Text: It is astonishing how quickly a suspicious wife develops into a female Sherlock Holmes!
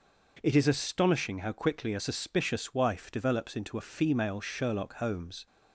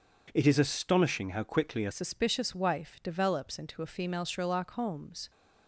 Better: first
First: none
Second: changes voice at "suspicious"; from 1.9 s on; 3.3 s long

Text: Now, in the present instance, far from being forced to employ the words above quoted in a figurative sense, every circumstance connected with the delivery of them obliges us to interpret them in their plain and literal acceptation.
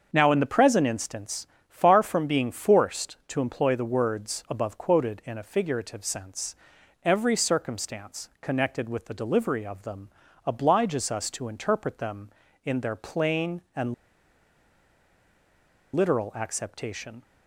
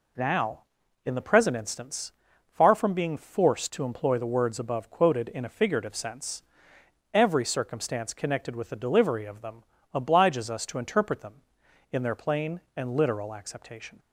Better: second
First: starts louder than the rest; until 1.1 s; 6.5 dB // pauses between "them" and "obliges"; slight; at 10.0 s; 0.36 s long // pauses between "and" and "literal"; strong; at 13.9 s; 2.0 s long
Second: pauses between "them" and "obliges"; slight; at 9.6 s; 0.30 s long

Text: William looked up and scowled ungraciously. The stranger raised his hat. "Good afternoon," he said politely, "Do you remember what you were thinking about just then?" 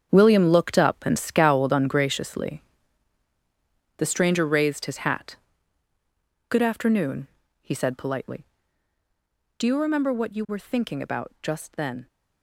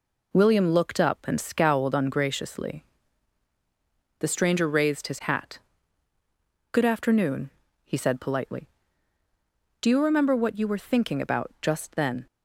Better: second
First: gets quieter; strong; throughout; 11.5 dB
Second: none

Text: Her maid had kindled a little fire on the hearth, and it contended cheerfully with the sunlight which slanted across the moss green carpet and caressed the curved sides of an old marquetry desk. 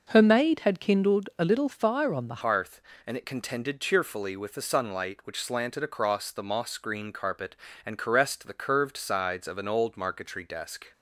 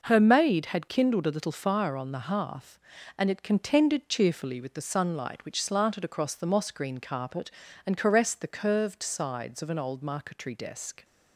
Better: second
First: changes voice at "hearth"; from 2.4 s on; 8.5 s long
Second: none

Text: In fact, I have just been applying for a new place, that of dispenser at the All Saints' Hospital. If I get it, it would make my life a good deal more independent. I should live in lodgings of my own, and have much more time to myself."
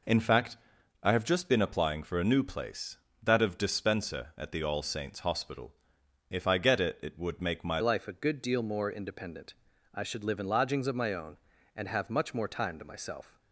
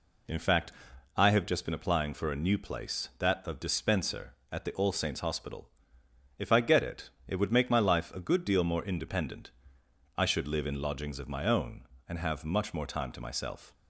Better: second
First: changes voice at "life"; from 7.8 s on; 5.5 s long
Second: none

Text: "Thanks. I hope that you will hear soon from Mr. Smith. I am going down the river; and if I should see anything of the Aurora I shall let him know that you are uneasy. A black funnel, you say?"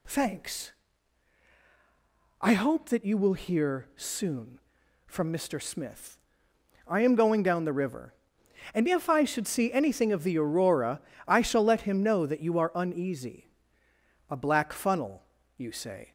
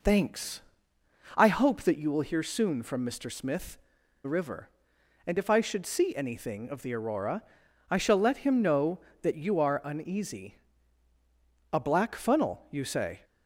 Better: first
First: pauses between "Aurora" and "I"; slight; at 11.0 s; 0.26 s long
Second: skips "I am going down"; at 4.0 s // pauses between "Aurora" and "I"; noticeable; at 7.4 s; 0.48 s long

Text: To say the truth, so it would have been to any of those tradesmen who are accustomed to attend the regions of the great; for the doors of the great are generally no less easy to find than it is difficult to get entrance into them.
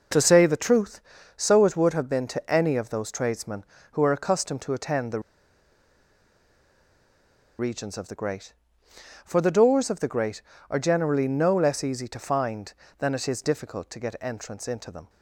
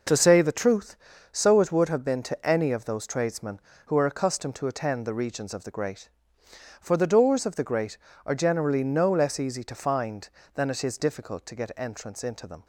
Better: second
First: pauses between "the" and "regions"; strong; at 5.2 s; 2.3 s long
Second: none

